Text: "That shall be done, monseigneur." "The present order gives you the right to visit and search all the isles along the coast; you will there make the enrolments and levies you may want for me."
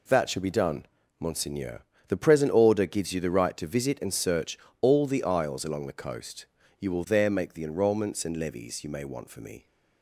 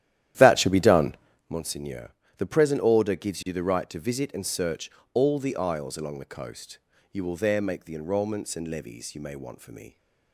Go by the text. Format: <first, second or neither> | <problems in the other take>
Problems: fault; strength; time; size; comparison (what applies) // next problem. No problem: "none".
first | starts louder than the rest; strong; until 1.6 s; 12 dB // pauses between "search" and "all"; slight; at 4.8 s; 0.24 s long; slight in the first